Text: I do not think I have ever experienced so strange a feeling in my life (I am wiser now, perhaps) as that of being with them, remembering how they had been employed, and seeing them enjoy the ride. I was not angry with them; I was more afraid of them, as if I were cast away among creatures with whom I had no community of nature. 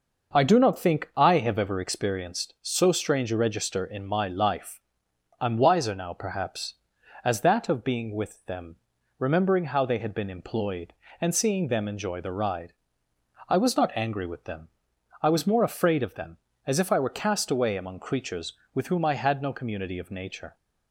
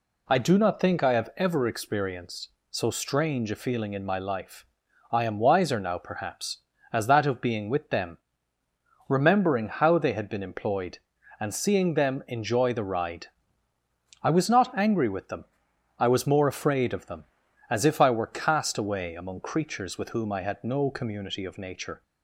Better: second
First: says "register" for "feeling"; at 3.3 s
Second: none

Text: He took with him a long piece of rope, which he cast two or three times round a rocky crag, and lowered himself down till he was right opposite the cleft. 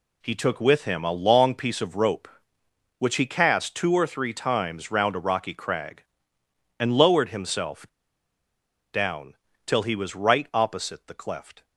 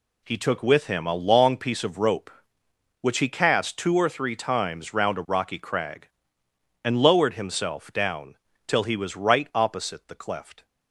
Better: second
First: pauses between "himself" and "down"; at 7.8 s; 1.0 s long // pauses between "down" and "till"; slight; at 9.3 s; 0.30 s long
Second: pauses between "down" and "till"; slight; at 8.3 s; 0.30 s long

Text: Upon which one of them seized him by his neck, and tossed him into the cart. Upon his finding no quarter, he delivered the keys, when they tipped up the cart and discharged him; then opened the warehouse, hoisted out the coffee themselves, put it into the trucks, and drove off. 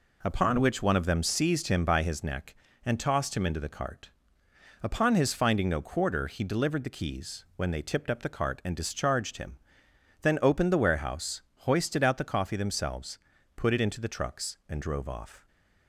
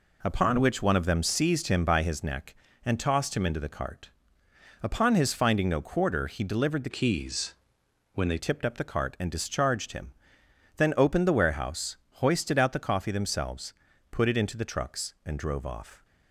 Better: first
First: none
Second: changes voice from "keys" to "they"; from 6.9 to 8.3 s; 1.4 s long

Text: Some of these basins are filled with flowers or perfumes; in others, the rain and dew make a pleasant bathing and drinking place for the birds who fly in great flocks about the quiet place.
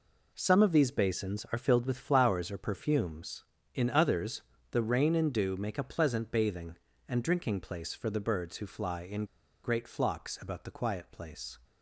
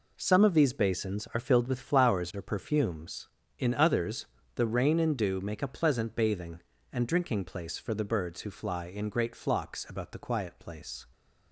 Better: second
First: pauses between "in" and "great"; at 9.2 s; 0.36 s long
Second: none

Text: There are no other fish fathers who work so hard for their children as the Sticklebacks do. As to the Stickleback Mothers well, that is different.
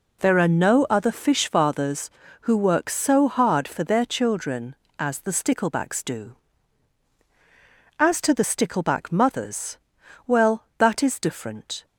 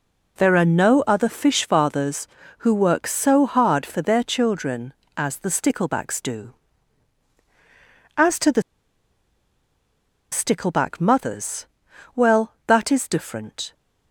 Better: first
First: pauses between "Mothers" and "well"; noticeable; at 9.7 s; 0.48 s long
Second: pauses between "the" and "Stickleback"; strong; at 8.6 s; 1.7 s long // pauses between "Mothers" and "well"; noticeable; at 11.6 s; 0.48 s long

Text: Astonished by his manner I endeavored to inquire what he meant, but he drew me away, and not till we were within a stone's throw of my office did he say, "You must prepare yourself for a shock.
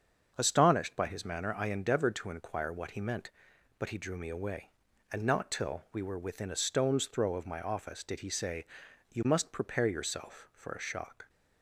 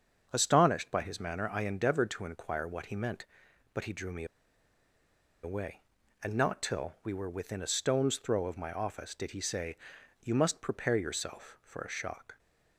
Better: first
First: starts louder than the rest; until 1.3 s; 7 dB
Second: starts louder than the rest; until 1.3 s; 7 dB // pauses between "me" and "away"; at 4.2 s; 1.1 s long

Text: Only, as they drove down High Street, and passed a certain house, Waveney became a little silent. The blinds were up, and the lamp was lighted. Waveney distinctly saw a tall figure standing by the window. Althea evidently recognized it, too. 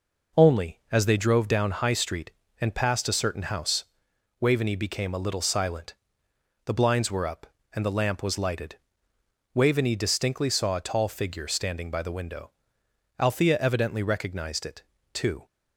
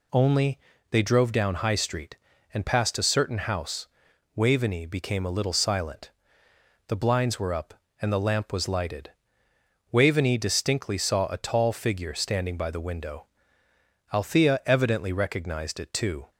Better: first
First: none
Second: skips "as"; at 0.7 s

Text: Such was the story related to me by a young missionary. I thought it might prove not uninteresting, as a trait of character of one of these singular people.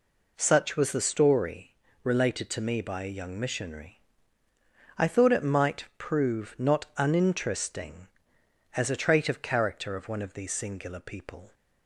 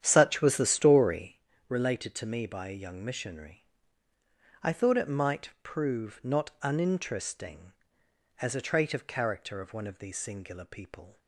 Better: first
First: pauses between "story" and "related"; slight; at 1.7 s; 0.30 s long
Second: starts louder than the rest; strong; until 1.4 s; 9.5 dB // pauses between "story" and "related"; slight; at 1.3 s; 0.30 s long

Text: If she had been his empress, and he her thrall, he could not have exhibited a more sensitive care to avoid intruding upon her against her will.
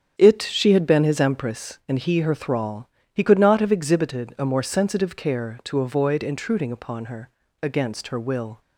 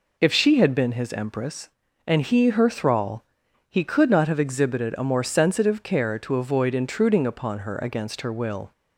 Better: second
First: starts louder than the rest; strong; until 1.1 s; 8 dB // says "It" for "If"; at 0.1 s // pauses between "her" and "against"; slight; at 7.2 s; 0.34 s long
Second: none

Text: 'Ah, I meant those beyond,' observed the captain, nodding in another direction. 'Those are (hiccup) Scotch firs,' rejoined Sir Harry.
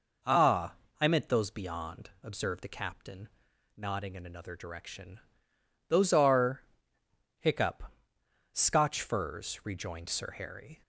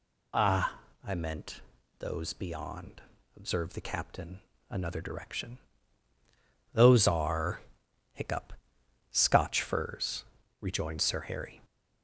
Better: first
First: none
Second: pauses between "meant" and "those"; at 1.6 s; 0.40 s long // skips "nodding in"; at 4.5 s

